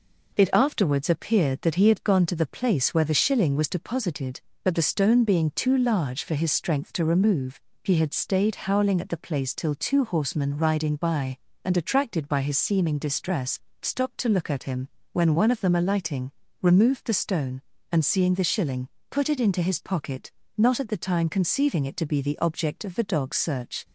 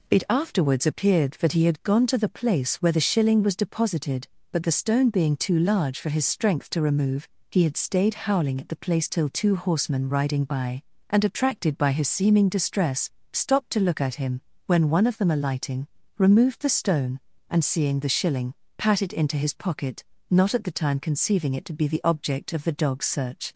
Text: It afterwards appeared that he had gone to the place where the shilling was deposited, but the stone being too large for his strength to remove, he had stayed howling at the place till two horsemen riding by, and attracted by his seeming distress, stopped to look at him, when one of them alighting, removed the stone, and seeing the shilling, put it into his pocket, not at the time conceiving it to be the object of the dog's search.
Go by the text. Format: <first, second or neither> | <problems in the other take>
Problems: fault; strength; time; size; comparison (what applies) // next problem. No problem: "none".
first | says "pat" for "put"; at 18.7 s